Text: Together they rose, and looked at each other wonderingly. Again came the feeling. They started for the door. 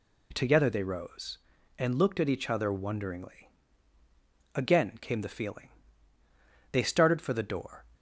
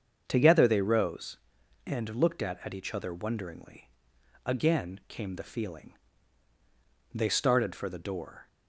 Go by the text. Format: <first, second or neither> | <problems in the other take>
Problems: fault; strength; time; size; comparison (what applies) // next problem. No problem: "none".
first | starts louder than the rest; until 1.2 s; 7 dB // says "at" twice; at 2.6 s